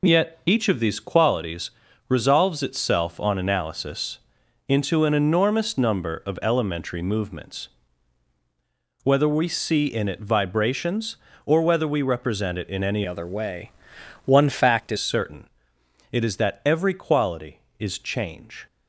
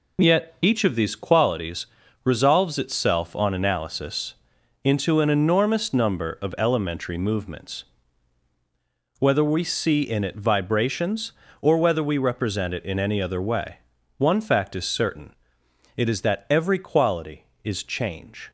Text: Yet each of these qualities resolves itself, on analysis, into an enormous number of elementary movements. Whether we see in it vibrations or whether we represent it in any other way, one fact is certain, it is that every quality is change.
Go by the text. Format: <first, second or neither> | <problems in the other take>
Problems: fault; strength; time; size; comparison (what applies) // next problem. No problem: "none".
second | pauses between "qualities" and "resolves"; at 1.7 s; 0.38 s long; also in the second // changes voice from "other" to "is"; from 13.0 to 14.9 s; 1.9 s long